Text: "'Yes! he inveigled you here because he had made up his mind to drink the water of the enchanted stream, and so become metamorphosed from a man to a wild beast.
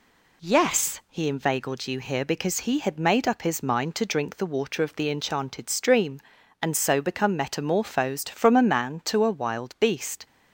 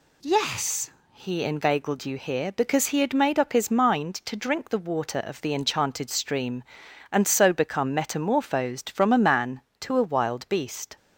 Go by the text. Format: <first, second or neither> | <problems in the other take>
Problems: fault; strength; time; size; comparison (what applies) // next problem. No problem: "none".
neither | none